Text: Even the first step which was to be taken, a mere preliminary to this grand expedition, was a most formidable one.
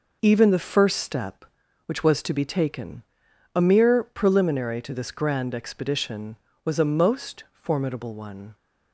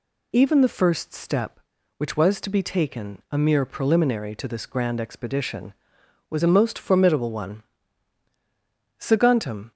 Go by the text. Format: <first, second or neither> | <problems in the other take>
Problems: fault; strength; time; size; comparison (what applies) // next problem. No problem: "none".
first | goes on to say "Saguntum"; noticeable; from 8.9 s on; 0.72 s long